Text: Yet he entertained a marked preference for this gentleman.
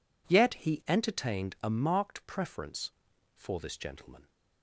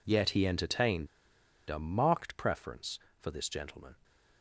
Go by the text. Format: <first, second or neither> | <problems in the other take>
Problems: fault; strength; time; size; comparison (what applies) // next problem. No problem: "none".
first | pauses between "entertained" and "a"; noticeable; at 1.0 s; 0.61 s long